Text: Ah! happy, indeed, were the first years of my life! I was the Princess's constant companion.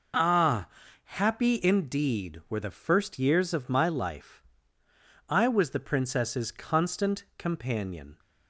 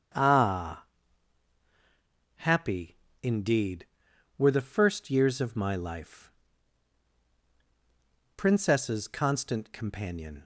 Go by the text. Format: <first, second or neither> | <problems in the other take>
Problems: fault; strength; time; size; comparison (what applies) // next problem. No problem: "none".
first | starts louder than the rest; strong; until 2.6 s; 8 dB // skips "I was the"; at 7.3 s